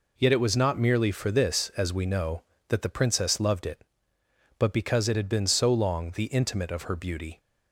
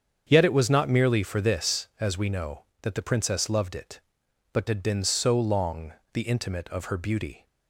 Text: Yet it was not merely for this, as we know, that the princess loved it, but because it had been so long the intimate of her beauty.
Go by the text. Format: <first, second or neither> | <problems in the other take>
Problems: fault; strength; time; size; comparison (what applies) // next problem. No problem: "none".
first | starts louder than the rest; strong; until 1.2 s; 7.5 dB // skips "because it"; at 4.6 s // pauses between "long" and "the"; slight; at 5.9 s; 0.20 s long